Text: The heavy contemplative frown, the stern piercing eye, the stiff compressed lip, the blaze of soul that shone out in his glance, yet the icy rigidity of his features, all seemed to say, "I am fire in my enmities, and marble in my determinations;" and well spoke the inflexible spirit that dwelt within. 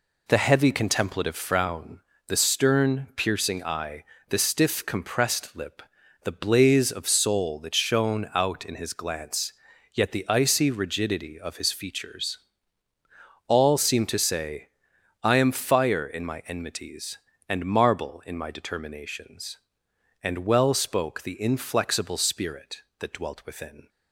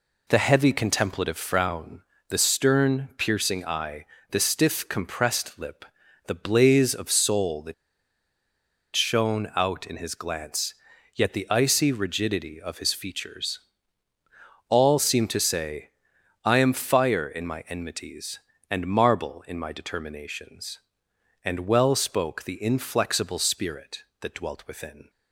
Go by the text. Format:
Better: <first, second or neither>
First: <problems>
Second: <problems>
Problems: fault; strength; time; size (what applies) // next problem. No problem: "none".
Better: first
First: none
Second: pauses between "that" and "shone"; at 7.7 s; 1.2 s long